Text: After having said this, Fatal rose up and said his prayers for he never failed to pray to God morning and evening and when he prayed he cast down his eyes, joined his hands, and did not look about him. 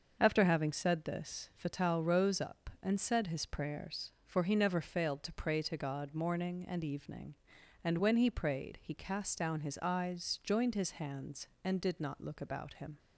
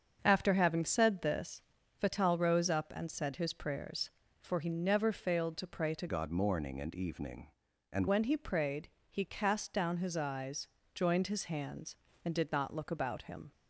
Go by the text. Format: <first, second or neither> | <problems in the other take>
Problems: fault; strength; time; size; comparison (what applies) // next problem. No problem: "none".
first | starts louder than the rest; until 1.2 s; 6.5 dB; also in the first // changes voice from "God" to "and"; from 6.0 to 8.0 s; 2.0 s long // pauses between "prayed" and "he"; slight; at 8.8 s; 0.20 s long